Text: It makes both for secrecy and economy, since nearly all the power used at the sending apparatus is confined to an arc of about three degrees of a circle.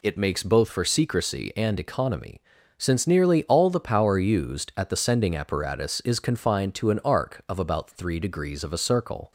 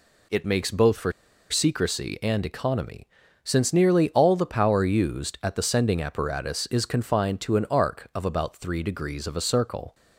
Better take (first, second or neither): first